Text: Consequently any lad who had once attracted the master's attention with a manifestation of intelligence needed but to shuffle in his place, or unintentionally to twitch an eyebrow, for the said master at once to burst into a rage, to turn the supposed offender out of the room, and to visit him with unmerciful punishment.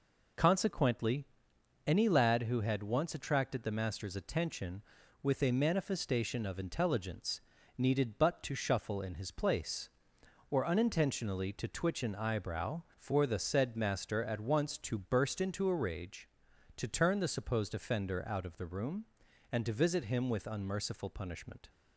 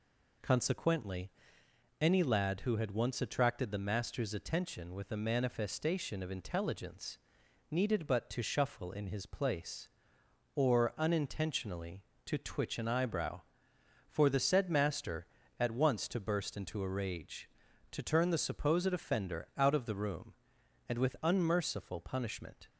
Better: first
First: pauses between "Consequently" and "any"; noticeable; at 1.2 s; 0.60 s long // pauses between "intelligence" and "needed"; slight; at 7.4 s; 0.36 s long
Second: pauses between "Consequently" and "any"; noticeable; at 1.3 s; 0.70 s long // pauses between "intelligence" and "needed"; noticeable; at 7.1 s; 0.52 s long // skips "to visit him"; at 20.9 s

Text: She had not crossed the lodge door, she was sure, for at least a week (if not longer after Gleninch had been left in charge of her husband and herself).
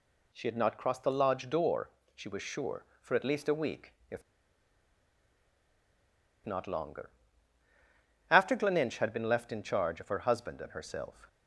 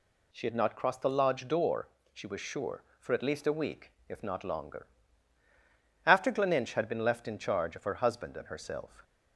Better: second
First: pauses between "if" and "not"; strong; at 4.2 s; 2.2 s long // pauses between "longer" and "after"; at 7.0 s; 1.2 s long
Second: pauses between "longer" and "after"; at 4.8 s; 1.1 s long

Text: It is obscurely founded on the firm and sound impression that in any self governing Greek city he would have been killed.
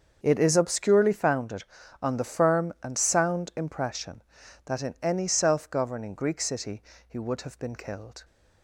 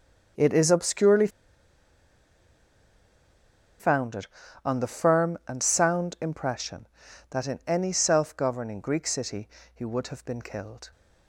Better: first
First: starts louder than the rest; until 1.2 s; 6.5 dB // pauses between "city" and "he"; slight; at 6.8 s; 0.24 s long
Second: starts louder than the rest; until 3.8 s; 6.5 dB // pauses between "obscurely" and "founded"; strong; at 1.2 s; 2.5 s long // pauses between "city" and "he"; slight; at 9.4 s; 0.24 s long

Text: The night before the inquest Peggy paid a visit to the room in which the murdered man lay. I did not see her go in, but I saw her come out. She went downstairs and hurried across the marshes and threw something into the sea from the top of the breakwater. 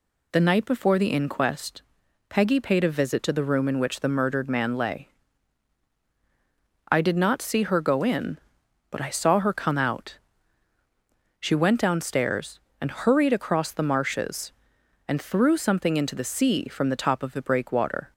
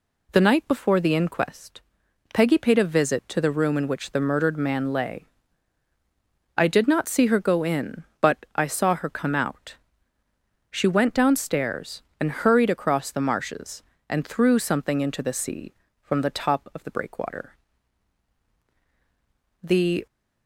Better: first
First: pauses between "inquest" and "Peggy"; noticeable; at 1.8 s; 0.46 s long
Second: pauses between "inquest" and "Peggy"; noticeable; at 1.7 s; 0.52 s long // goes on to say "The"; slight; from 19.6 s on; 0.42 s long

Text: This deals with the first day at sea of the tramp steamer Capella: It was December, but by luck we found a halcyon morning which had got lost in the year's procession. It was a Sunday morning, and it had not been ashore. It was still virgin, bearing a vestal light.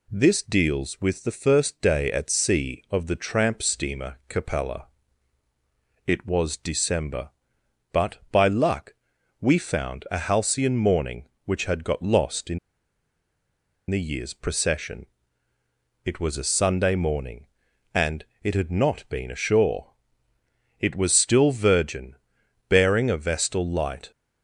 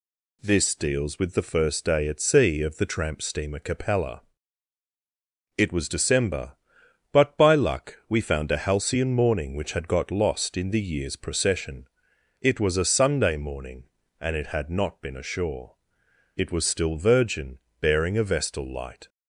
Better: second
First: pauses between "luck" and "we"; at 8.9 s; 0.44 s long // pauses between "in" and "the"; strong; at 12.5 s; 1.3 s long // pauses between "and" and "it"; slight; at 18.2 s; 0.18 s long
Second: none

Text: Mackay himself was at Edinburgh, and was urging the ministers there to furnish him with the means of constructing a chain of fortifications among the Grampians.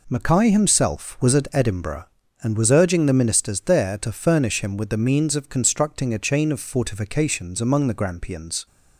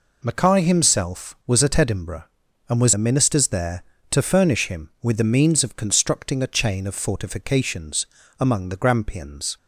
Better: first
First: none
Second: skips "urging"; at 2.9 s // pauses between "fortifications" and "among"; slight; at 8.0 s; 0.36 s long

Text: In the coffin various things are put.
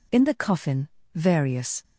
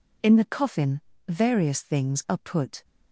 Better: second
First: pauses between "coffin" and "various"; slight; at 0.8 s; 0.28 s long // stops before "things are put"; at 1.8 s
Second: pauses between "coffin" and "various"; slight; at 1.0 s; 0.26 s long

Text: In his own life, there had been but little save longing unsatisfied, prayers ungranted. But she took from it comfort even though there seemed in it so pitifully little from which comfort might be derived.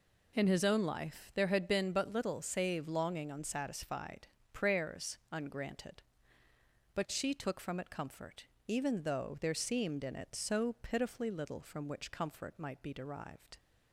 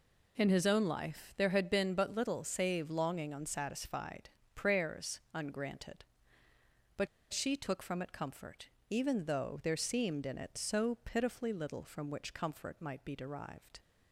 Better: first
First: pauses between "comfort" and "even"; slight; at 8.4 s; 0.22 s long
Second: pauses between "But" and "she"; slight; at 7.0 s; 0.25 s long // pauses between "comfort" and "even"; slight; at 8.6 s; 0.22 s long

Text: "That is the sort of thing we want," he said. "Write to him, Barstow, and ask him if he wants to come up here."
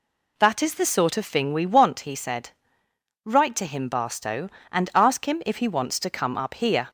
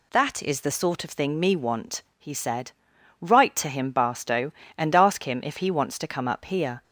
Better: first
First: none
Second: says "me" for "we"; at 1.3 s

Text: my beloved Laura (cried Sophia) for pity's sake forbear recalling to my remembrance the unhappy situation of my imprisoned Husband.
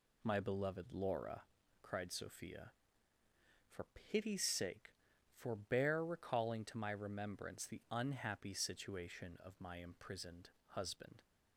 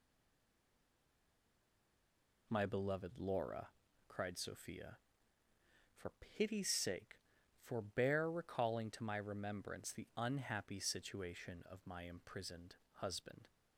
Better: first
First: pauses between "for" and "pity's"; slight; at 3.8 s; 0.26 s long // pauses between "sake" and "forbear"; noticeable; at 4.8 s; 0.48 s long // pauses between "imprisoned" and "Husband"; slight; at 10.4 s; 0.24 s long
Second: stays silent before the first word; until 2.4 s; 2.4 s long // pauses between "for" and "pity's"; slight; at 6.1 s; 0.26 s long // pauses between "sake" and "forbear"; noticeable; at 7.1 s; 0.48 s long // pauses between "imprisoned" and "Husband"; slight; at 12.7 s; 0.24 s long

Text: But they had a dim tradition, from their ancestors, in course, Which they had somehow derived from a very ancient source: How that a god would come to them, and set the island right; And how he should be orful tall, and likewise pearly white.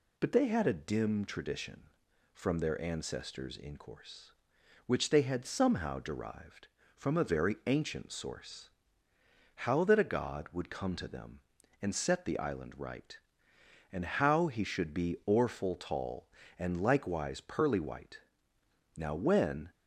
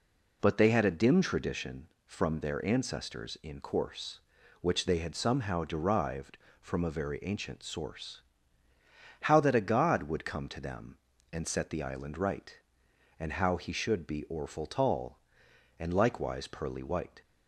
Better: second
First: goes on to say "Now when"; noticeable; from 18.9 s on; 0.74 s long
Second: none

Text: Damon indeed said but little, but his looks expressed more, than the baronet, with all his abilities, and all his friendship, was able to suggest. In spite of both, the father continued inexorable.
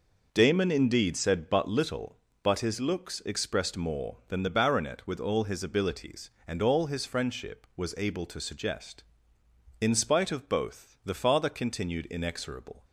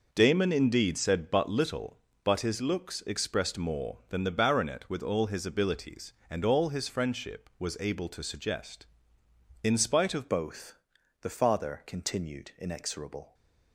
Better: first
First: none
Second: changes voice at "both"; from 10.2 s on; 3.1 s long

